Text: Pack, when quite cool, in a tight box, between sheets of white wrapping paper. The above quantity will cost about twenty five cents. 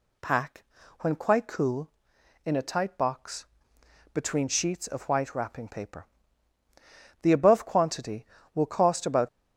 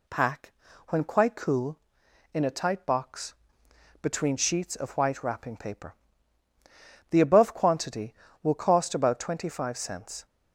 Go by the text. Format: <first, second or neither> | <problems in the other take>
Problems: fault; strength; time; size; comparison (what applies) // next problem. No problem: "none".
second | stops before "twenty five cents"; at 9.2 s